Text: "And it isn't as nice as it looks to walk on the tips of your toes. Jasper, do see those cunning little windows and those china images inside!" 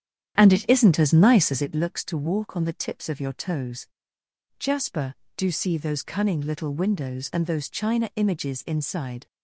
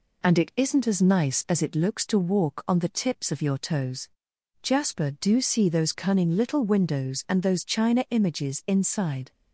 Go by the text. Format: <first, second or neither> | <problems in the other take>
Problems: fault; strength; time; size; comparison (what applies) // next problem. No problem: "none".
second | starts louder than the rest; strong; until 1.7 s; 9.5 dB